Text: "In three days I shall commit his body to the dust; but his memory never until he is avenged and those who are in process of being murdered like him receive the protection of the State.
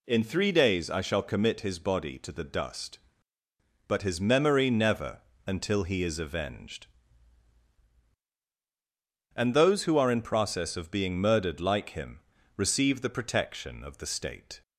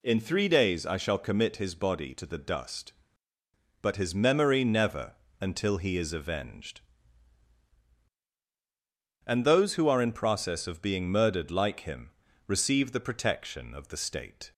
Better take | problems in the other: neither | pauses between "never" and "until"; slight; the same in both // pauses between "him" and "receive"; slight; the same in both

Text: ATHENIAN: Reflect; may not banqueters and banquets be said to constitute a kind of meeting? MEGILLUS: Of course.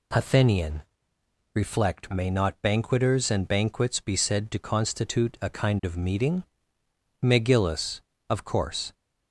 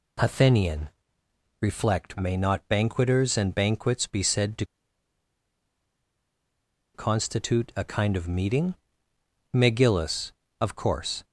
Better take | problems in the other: first | pauses between "to" and "constitute"; strong; at 4.6 s; 2.2 s long

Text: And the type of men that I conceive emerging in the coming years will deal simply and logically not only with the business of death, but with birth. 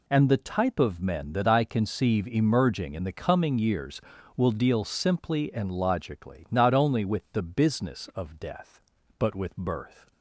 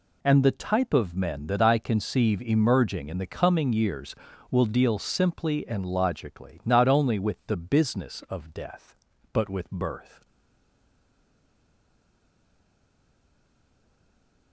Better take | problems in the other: first | stays silent after the last word; strong; from 10.2 s on; 4.3 s long

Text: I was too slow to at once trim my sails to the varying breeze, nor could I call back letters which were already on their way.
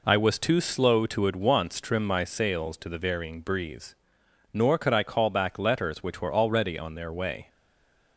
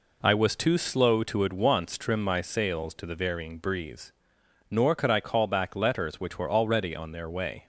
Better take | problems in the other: second | stays silent after the last word; slight; from 7.4 s on; 0.7 s long

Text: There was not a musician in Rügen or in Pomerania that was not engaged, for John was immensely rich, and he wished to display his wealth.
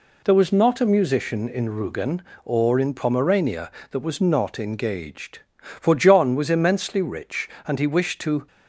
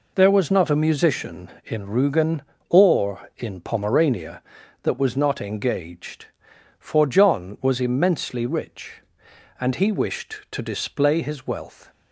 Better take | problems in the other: second | stops before "display his wealth"; at 8.4 s

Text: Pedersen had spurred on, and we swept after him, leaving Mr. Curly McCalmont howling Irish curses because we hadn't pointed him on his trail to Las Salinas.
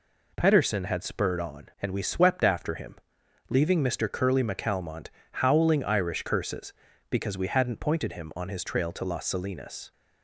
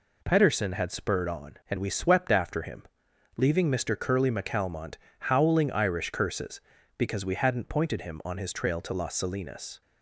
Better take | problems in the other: neither | pauses between "McCalmont" and "howling"; slight; the same in both

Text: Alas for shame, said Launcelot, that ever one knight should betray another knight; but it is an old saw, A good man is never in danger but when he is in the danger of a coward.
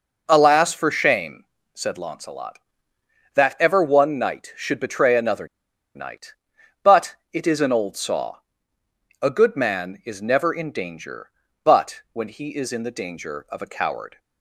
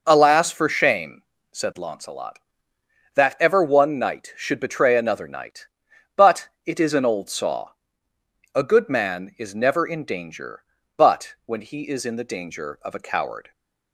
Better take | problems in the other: second | pauses between "another" and "knight"; noticeable; at 5.4 s; 0.48 s long // pauses between "but" and "it"; slight; at 7.1 s; 0.16 s long; slight in the second

